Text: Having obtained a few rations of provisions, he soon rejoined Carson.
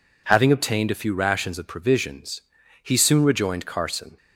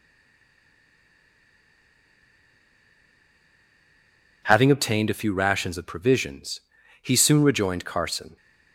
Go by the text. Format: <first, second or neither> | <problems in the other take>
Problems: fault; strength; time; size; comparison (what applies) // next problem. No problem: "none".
first | stays silent before the first word; strong; until 4.4 s; 4.4 s long